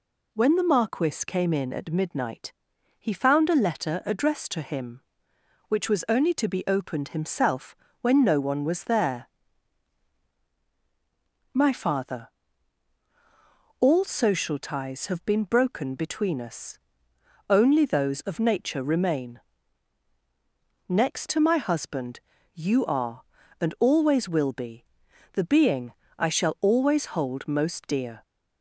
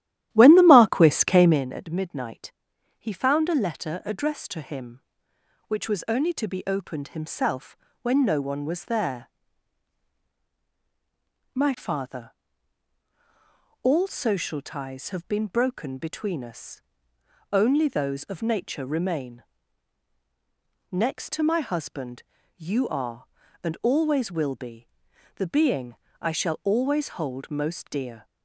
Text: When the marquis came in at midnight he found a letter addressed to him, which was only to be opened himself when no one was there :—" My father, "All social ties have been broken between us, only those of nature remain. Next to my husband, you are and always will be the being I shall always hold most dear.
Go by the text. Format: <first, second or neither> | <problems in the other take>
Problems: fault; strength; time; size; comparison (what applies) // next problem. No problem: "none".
first | starts louder than the rest; strong; until 1.7 s; 13.5 dB // pauses between "midnight" and "he"; at 2.5 s; 0.44 s long; also in the first // pauses between "himself" and "when"; slight; at 7.7 s; 0.26 s long; slight in the first // pauses between "be" and "the"; noticeable; at 24.8 s; 0.46 s long; noticeable in the first // pauses between "being" and "I"; slight; at 25.9 s; 0.28 s long; slight in the first